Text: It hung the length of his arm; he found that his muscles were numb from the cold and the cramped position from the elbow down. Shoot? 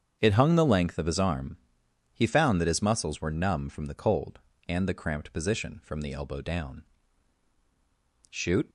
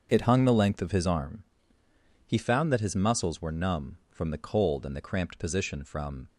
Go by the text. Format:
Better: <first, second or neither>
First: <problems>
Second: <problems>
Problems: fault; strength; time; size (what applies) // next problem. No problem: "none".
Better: first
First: starts louder than the rest; strong; until 1.2 s; 7.5 dB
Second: starts louder than the rest; until 1.1 s; 6.5 dB // stops before "the elbow down Shoot"; at 6.2 s